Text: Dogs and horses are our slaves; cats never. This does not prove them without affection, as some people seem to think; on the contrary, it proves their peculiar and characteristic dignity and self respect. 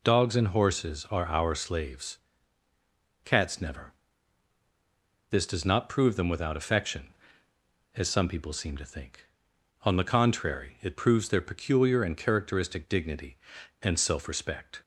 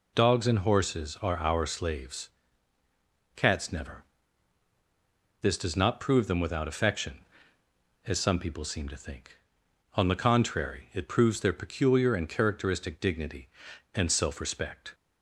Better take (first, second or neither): neither